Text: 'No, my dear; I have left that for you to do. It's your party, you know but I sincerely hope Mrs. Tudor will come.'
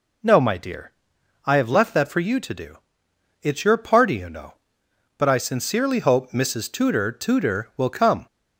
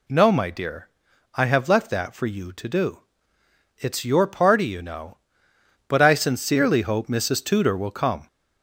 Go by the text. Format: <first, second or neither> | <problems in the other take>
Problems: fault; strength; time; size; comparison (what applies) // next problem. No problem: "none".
second | says "Tudor" twice; at 7.1 s